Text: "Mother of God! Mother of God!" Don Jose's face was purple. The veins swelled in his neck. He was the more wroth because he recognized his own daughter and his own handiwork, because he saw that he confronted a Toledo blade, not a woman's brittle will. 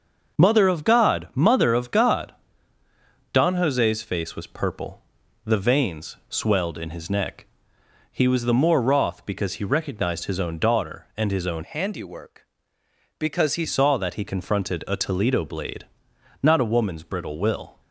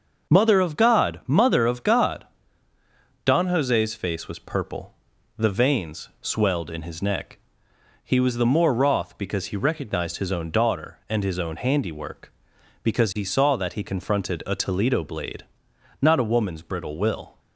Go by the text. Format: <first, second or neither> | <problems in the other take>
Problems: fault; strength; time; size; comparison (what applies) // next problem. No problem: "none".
second | starts louder than the rest; noticeable; until 1.4 s; 6 dB; noticeable in the second // changes voice from "handiwork" to "he"; from 11.6 to 13.6 s; 2.0 s long